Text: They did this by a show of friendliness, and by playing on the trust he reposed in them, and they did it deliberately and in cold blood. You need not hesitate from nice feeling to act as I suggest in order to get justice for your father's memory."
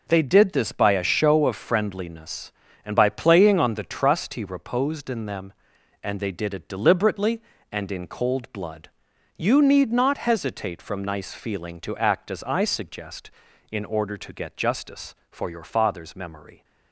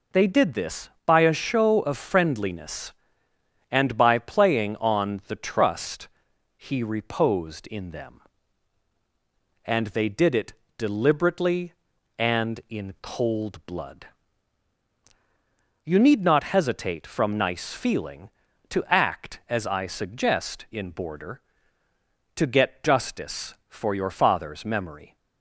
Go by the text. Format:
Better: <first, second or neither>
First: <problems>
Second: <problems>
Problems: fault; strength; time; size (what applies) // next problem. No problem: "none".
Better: first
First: none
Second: pauses between "trust" and "he"; noticeable; at 6.0 s; 0.48 s long // pauses between "it" and "deliberately"; slight; at 10.5 s; 0.24 s long // says "border" for "order"; at 20.9 s